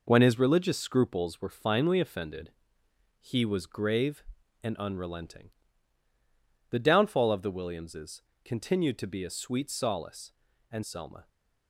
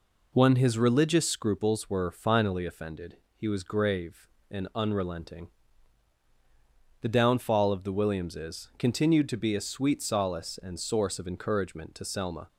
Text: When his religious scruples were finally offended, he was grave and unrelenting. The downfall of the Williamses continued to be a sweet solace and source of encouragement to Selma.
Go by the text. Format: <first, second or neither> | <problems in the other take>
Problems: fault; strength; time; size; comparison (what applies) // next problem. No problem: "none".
second | pauses between "Williamses" and "continued"; slight; at 8.2 s; 0.20 s long // skips "source of encouragement to"; at 10.8 s